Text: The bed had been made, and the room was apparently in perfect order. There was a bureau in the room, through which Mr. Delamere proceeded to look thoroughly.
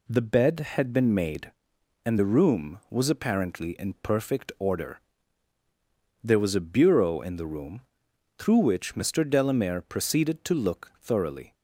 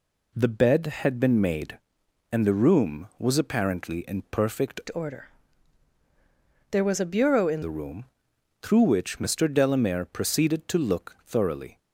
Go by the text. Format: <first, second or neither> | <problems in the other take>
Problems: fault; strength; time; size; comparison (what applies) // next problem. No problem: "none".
first | changes voice from "order" to "in"; from 4.9 to 7.6 s; 2.7 s long